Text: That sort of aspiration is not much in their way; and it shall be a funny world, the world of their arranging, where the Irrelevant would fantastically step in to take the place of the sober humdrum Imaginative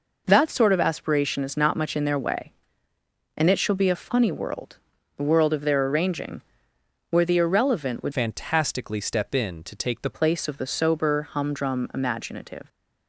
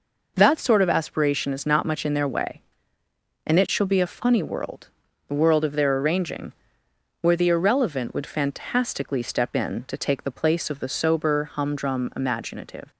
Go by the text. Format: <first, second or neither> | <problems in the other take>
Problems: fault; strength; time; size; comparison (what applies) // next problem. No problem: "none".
second | changes voice from "fantastically" to "the"; from 8.1 to 10.1 s; 2.0 s long